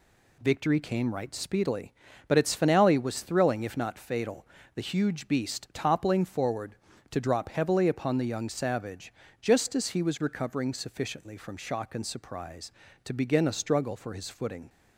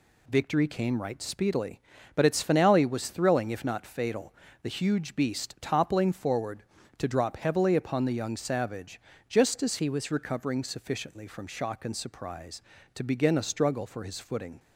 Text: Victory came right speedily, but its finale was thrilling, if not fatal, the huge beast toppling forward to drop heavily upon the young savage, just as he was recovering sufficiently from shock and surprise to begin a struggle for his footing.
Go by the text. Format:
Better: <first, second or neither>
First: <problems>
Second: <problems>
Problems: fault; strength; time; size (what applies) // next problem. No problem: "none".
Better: first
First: none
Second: changes voice from "he" to "was"; from 9.7 to 10.1 s; 0.4 s long